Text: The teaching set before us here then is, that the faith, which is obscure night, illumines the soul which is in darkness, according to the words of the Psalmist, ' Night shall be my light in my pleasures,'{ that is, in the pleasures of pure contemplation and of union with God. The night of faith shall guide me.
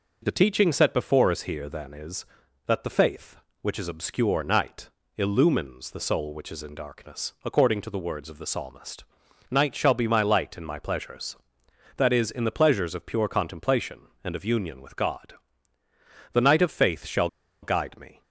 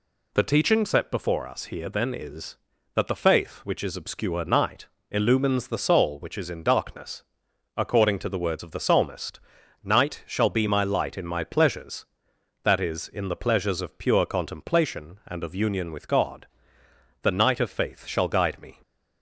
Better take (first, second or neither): second